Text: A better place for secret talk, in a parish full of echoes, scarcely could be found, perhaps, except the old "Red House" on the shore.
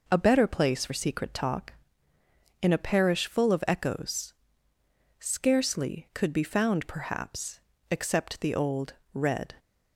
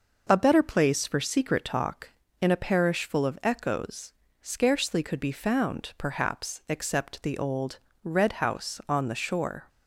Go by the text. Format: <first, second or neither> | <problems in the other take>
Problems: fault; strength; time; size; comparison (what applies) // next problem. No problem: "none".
second | pauses between "old" and "Red"; slight; at 8.9 s; 0.21 s long; slight in the second // stops before "House on the shore"; at 9.5 s